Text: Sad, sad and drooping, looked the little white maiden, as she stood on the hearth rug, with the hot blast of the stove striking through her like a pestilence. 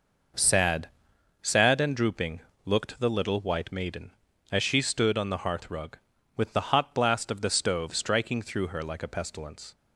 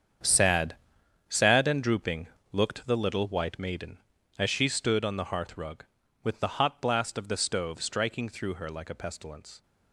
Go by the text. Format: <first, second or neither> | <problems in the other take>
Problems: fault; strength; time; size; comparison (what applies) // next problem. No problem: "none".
first | gets quieter; strong; throughout; 12 dB